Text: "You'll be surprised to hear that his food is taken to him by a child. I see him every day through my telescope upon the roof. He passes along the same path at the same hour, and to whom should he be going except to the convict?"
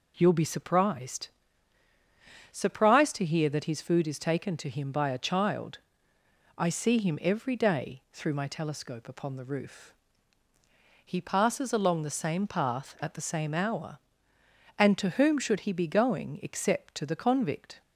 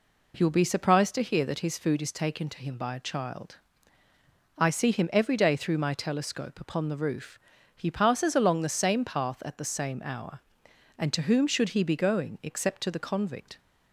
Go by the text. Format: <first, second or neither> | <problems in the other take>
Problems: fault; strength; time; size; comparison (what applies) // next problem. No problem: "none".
second | says "surprised" twice; at 2.5 s